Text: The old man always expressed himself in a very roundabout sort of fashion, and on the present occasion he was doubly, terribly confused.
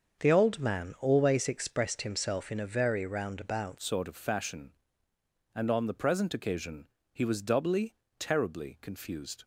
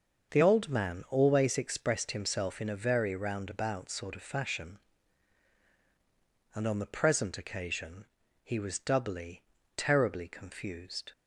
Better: second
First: starts louder than the rest; until 1.2 s; 7 dB // changes voice at "sort"; from 3.7 s on; 5.7 s long // pauses between "occasion" and "he"; slight; at 6.8 s; 0.26 s long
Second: starts louder than the rest; until 1.3 s; 6.5 dB // pauses between "occasion" and "he"; slight; at 8.0 s; 0.36 s long

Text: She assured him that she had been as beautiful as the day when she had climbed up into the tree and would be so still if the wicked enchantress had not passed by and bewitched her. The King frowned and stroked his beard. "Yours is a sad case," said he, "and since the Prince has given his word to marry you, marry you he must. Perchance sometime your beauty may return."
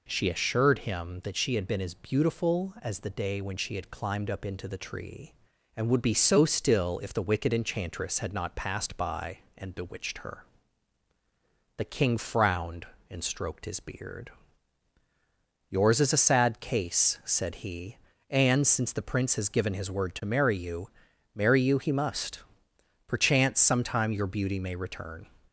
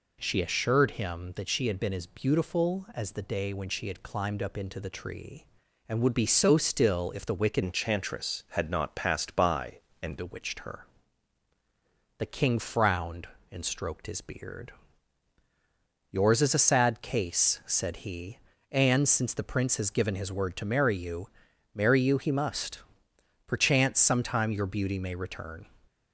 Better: first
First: none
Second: changes voice from "enchantress" to "and"; from 7.6 to 10.1 s; 2.5 s long

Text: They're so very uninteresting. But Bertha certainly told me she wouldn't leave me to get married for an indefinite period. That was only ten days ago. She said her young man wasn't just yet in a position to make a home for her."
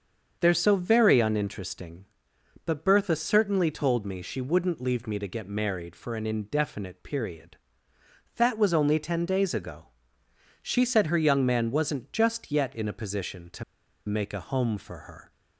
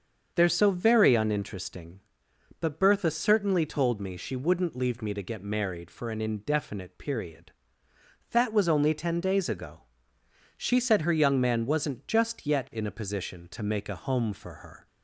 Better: second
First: starts louder than the rest; until 1.4 s; 7 dB // pauses between "to" and "make"; at 13.6 s; 0.42 s long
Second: starts louder than the rest; until 1.3 s; 7 dB

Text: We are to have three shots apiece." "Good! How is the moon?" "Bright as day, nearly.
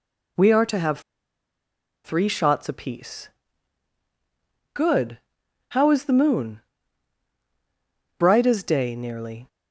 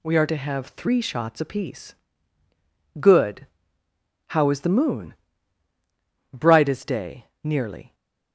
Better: second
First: pauses between "have" and "three"; at 0.9 s; 1.0 s long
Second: none

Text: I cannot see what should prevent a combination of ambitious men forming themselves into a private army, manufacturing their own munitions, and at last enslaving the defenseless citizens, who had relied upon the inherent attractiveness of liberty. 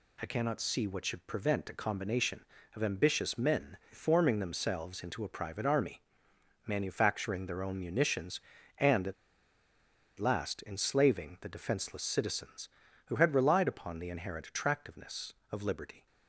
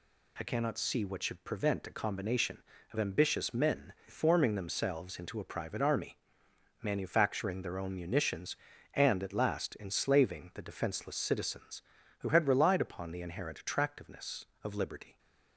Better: second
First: pauses between "at" and "last"; at 9.1 s; 1.0 s long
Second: none

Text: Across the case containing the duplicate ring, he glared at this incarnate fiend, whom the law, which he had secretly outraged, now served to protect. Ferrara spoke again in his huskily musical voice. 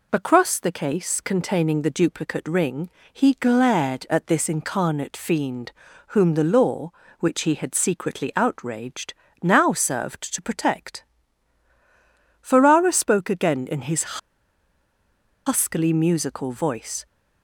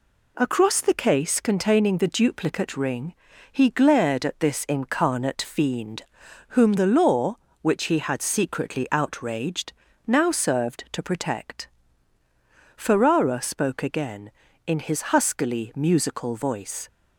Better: second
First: pauses between "his" and "huskily"; strong; at 14.1 s; 1.2 s long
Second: none

